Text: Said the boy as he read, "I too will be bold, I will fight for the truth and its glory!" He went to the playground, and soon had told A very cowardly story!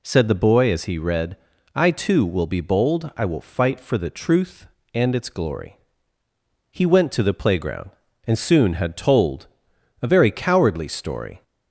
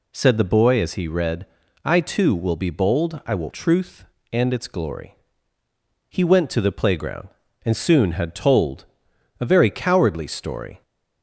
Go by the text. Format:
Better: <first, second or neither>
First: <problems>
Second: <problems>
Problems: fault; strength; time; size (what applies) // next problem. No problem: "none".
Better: first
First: pauses between "told" and "A"; noticeable; at 9.4 s; 0.58 s long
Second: skips "fight for the"; at 3.4 s // pauses between "told" and "A"; noticeable; at 8.8 s; 0.58 s long